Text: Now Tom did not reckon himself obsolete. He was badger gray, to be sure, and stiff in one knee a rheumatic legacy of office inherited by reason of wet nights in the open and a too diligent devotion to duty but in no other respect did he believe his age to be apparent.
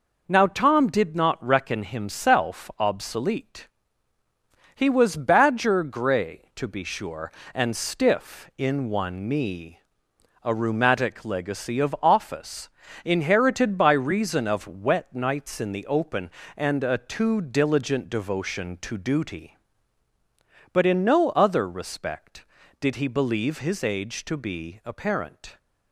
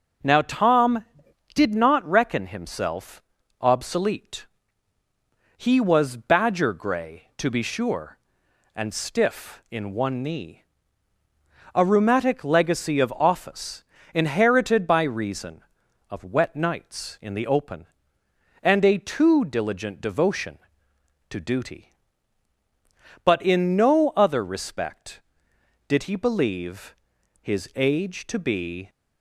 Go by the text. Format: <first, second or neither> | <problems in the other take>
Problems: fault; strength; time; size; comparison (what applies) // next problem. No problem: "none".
first | pauses between "himself" and "obsolete"; at 3.2 s; 0.38 s long // pauses between "knee" and "a"; at 10.5 s; 1.1 s long; noticeable in the first // pauses between "office" and "inherited"; slight; at 13.8 s; 0.32 s long; also in the first // pauses between "believe" and "his"; noticeable; at 26.9 s; 0.48 s long // stops before "apparent"; at 28.8 s